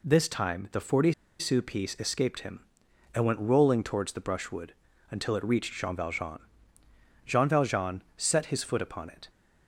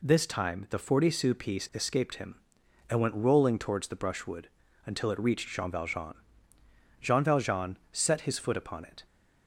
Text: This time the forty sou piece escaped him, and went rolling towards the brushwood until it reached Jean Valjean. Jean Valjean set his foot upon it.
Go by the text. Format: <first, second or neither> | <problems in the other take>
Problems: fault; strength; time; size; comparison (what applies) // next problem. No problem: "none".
second | pauses between "forty" and "sou"; slight; at 1.1 s; 0.25 s long // pauses between "brushwood" and "until"; slight; at 4.7 s; 0.36 s long; slight in the second